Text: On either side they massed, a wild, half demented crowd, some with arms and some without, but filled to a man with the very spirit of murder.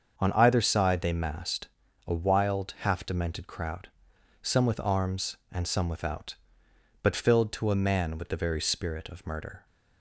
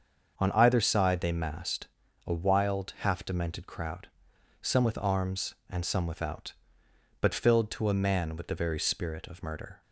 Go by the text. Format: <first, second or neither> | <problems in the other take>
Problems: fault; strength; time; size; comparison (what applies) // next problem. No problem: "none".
neither | starts louder than the rest; the same in both